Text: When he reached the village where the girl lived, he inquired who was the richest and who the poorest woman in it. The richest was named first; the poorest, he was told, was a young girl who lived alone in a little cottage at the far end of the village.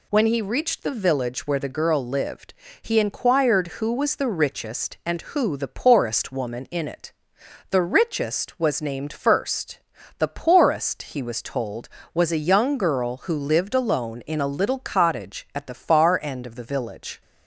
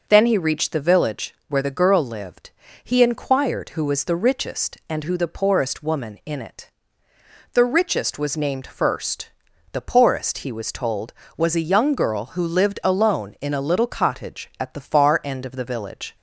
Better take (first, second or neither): first